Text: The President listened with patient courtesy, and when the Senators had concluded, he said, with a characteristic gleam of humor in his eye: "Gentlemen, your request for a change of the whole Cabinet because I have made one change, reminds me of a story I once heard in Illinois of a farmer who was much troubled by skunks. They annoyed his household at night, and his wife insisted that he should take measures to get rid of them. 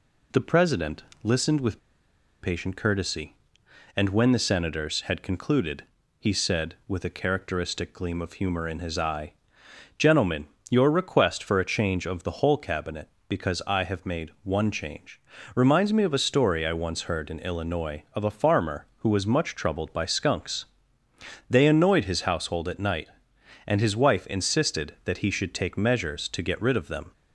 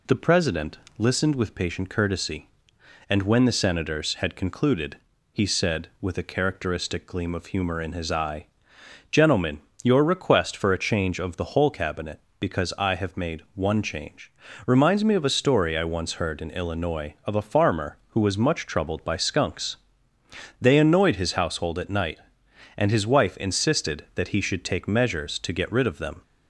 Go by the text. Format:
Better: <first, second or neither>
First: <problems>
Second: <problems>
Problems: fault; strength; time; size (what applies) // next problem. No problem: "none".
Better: second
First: pauses between "President" and "listened"; slight; at 1.0 s; 0.22 s long // pauses between "with" and "patient"; noticeable; at 1.7 s; 0.62 s long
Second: pauses between "President" and "listened"; slight; at 0.7 s; 0.22 s long